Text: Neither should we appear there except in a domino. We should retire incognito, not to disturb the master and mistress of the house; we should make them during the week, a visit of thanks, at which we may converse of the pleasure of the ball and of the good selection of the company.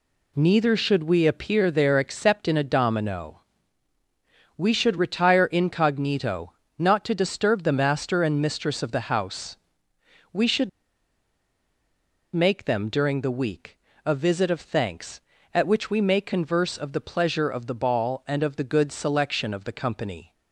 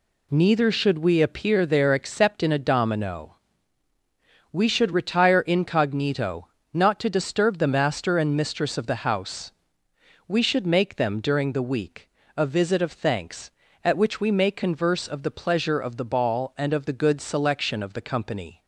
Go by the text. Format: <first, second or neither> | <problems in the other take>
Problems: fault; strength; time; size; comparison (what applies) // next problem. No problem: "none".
second | pauses between "should" and "make"; strong; at 10.6 s; 1.6 s long